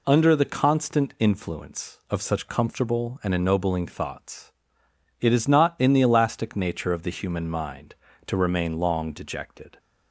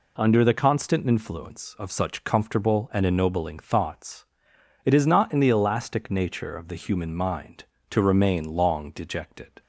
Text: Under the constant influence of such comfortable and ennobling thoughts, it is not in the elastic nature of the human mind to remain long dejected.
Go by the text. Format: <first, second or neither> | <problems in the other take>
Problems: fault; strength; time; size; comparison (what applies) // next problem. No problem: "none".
neither | none